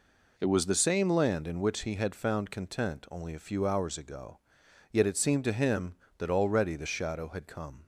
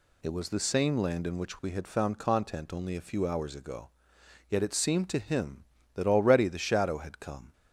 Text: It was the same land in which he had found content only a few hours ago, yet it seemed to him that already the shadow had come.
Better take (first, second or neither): first